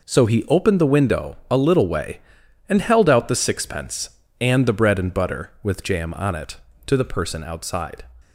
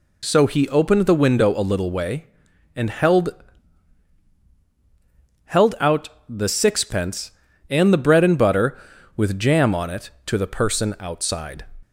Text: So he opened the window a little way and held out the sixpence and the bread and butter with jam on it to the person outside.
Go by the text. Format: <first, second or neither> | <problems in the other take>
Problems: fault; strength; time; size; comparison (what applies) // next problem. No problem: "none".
first | says "held" twice; at 5.4 s // pauses between "out" and "the"; slight; at 6.0 s; 0.22 s long